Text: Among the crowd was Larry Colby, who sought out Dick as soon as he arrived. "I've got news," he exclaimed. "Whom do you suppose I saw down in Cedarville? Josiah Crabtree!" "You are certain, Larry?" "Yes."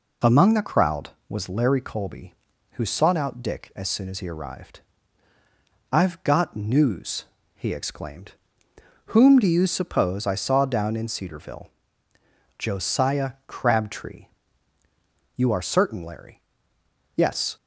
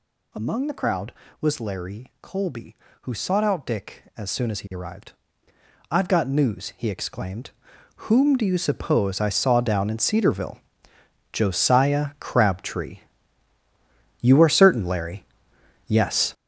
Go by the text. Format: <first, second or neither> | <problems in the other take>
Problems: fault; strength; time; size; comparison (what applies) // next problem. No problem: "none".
first | gets louder; strong; throughout; 9.5 dB